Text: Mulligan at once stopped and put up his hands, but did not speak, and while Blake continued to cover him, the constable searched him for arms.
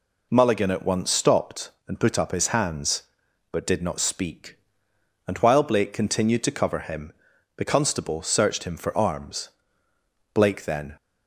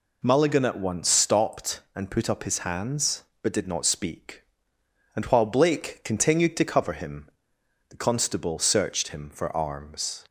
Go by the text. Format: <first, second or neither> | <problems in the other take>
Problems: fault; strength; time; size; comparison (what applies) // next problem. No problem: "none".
second | goes on to say "Blake then"; noticeable; from 10.3 s on; 0.62 s long